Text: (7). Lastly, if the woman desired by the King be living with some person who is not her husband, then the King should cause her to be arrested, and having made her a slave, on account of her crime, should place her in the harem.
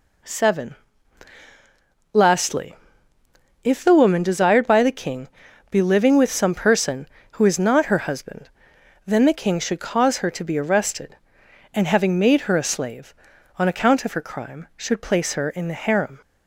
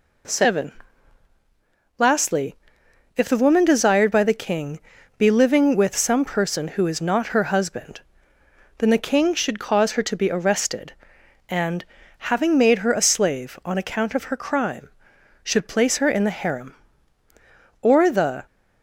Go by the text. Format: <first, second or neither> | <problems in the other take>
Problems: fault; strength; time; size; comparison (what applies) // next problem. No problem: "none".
first | pauses between "King" and "be"; at 4.7 s; 0.38 s long; also in the first // pauses between "and" and "having"; slight; at 11.8 s; 0.34 s long // goes on to say "Or the"; noticeable; from 17.7 s on; 0.66 s long